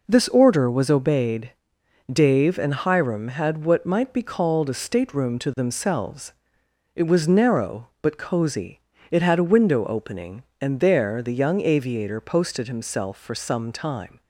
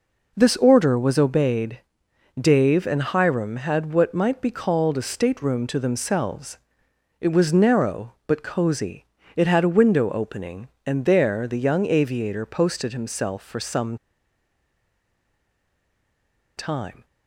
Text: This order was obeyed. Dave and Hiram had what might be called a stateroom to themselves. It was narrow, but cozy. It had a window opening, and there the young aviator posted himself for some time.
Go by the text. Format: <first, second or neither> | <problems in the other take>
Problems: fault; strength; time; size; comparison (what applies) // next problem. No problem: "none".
first | pauses between "some" and "time"; strong; at 13.9 s; 2.6 s long